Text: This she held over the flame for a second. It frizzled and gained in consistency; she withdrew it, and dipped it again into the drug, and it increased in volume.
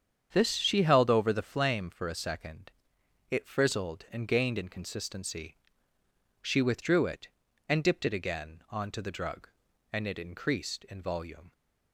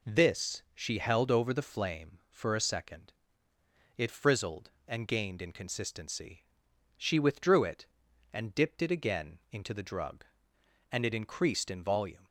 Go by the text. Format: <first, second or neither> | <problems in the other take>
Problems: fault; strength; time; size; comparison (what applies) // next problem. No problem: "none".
second | starts louder than the rest; strong; until 1.3 s; 8 dB // says "onto" for "into"; at 8.6 s